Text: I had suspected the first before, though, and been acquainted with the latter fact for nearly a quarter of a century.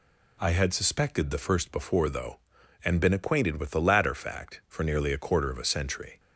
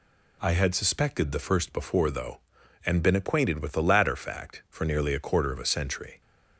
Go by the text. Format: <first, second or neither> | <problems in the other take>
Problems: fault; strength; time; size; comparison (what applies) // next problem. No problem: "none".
neither | none